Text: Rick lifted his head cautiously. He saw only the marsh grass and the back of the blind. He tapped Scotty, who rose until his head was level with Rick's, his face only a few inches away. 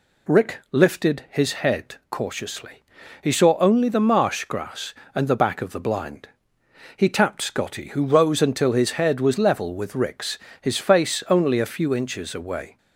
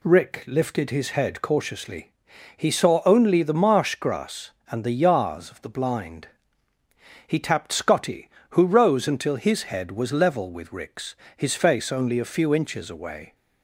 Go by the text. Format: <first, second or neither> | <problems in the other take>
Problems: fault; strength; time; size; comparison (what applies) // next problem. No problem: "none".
first | says "yars" for "back"; at 5.0 s